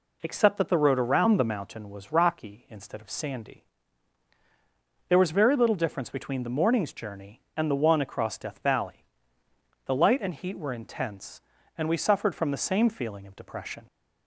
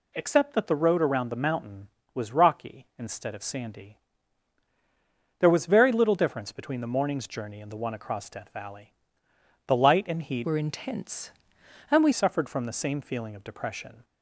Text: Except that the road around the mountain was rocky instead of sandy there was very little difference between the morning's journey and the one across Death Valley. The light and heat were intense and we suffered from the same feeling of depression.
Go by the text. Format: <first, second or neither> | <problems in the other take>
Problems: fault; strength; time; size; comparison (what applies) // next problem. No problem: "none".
first | pauses between "sandy" and "there"; strong; at 3.9 s; 1.4 s long; strong in the first // changes voice from "were" to "we"; from 10.4 to 12.1 s; 1.7 s long